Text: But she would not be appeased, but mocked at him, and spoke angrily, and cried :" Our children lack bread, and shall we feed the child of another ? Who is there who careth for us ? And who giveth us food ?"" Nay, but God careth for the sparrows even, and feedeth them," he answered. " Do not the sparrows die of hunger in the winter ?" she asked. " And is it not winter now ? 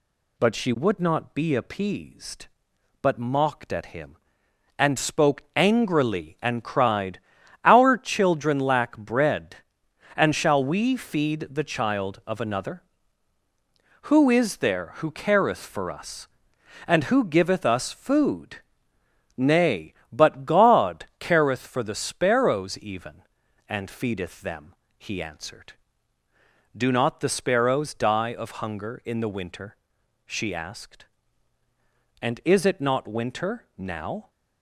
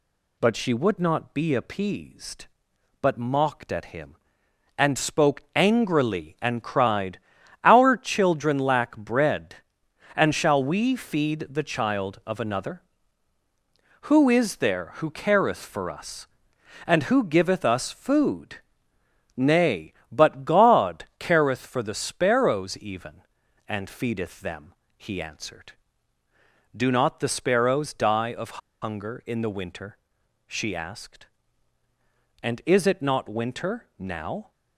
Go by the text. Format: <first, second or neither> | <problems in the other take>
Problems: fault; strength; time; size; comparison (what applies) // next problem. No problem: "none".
first | pauses between "of" and "hunger"; slight; at 28.6 s; 0.22 s long